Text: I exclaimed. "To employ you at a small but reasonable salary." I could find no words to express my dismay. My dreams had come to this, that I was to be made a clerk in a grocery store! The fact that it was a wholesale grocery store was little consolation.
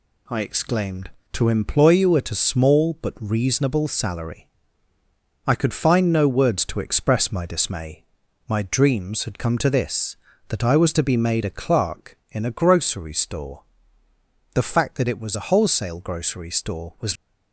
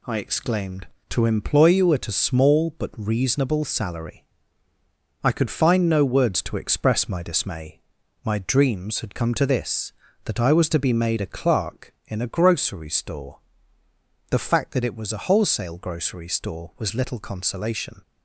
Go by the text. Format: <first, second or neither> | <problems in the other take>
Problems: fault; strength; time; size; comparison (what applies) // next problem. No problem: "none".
second | stops before "little consolation"; at 17.1 s